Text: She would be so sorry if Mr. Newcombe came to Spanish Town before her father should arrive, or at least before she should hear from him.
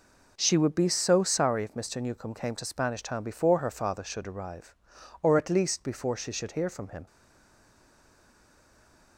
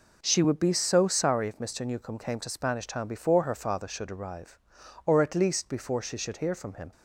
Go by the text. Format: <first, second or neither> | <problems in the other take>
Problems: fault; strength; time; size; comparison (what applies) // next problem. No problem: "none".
second | stays silent after the last word; from 7.0 s on; 2.1 s long